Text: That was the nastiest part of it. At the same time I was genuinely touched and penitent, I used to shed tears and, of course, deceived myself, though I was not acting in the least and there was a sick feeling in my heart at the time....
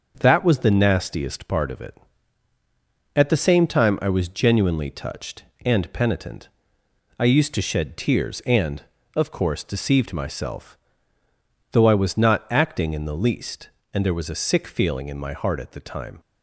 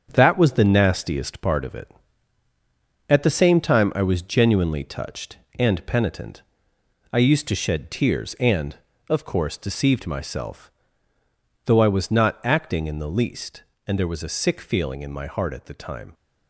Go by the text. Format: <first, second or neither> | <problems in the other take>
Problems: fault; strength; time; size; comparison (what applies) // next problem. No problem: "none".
first | gets quieter; throughout; 6.5 dB // starts louder than the rest; strong; until 1.1 s; 7.5 dB; also in the first